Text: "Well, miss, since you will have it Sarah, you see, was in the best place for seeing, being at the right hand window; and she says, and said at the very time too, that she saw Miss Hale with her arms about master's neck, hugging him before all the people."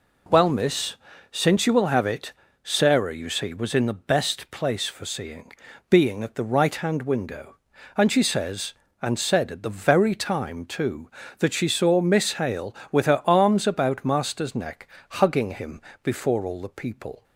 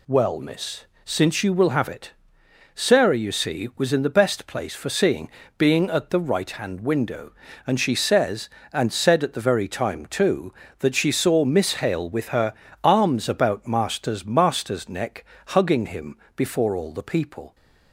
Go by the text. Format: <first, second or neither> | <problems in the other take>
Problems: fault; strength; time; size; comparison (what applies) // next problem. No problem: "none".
first | pauses between "it" and "Sarah"; noticeable; at 2.1 s; 0.64 s long; slight in the first // pauses between "her" and "arms"; slight; at 12.5 s; 0.30 s long // says "master's" twice; at 14.2 s // pauses between "him" and "before"; slight; at 16.1 s; 0.18 s long; slight in the first